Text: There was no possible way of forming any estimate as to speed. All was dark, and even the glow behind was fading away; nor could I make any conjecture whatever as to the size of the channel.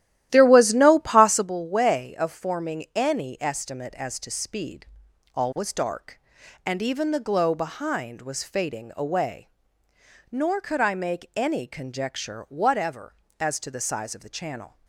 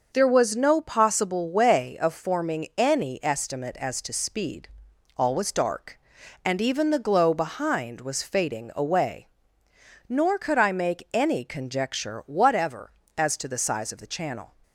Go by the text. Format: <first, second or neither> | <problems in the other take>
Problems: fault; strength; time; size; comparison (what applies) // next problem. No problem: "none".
second | starts louder than the rest; strong; until 1.5 s; 13 dB